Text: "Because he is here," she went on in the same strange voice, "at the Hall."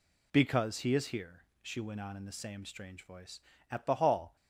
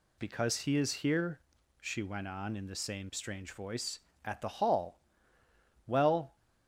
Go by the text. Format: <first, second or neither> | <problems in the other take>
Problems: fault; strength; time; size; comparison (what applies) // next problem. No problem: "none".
first | goes on to say "Well"; slight; from 5.8 s on; 0.48 s long